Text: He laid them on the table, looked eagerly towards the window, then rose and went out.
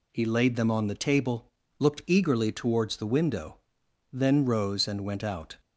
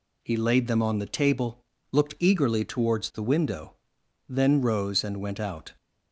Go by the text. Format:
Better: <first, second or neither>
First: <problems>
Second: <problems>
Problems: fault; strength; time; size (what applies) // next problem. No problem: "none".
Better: neither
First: none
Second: none